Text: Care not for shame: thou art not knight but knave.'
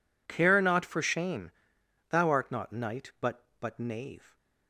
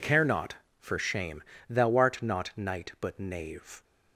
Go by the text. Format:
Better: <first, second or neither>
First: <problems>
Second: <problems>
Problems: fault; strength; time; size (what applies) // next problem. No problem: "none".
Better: second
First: says "but" twice; at 3.5 s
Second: none